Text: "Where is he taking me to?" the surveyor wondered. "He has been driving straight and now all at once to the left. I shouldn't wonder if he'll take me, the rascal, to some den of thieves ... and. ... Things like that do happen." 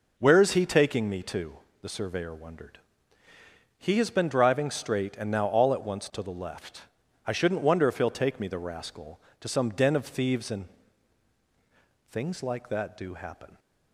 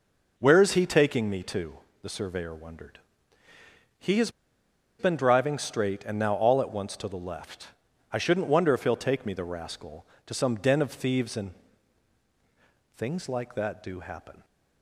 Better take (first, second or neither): first